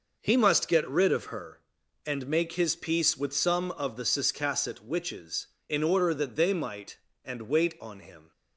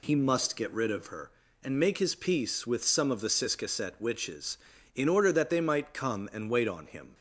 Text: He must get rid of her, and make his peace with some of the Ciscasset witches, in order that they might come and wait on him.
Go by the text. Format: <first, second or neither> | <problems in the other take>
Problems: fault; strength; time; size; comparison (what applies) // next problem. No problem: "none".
second | skips "come"; at 7.1 s